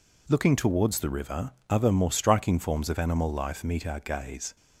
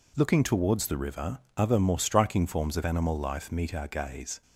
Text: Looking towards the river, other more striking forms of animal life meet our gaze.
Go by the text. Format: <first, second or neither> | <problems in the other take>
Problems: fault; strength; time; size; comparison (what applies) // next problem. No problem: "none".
neither | none